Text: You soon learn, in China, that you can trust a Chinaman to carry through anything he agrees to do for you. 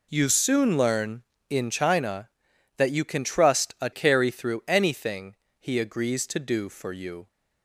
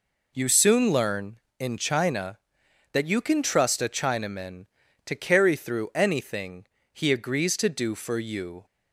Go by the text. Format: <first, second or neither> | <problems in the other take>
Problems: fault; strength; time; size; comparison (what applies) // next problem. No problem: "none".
second | skips "Chinaman to"; at 3.9 s // pauses between "anything" and "he"; slight; at 5.3 s; 0.24 s long; slight in the second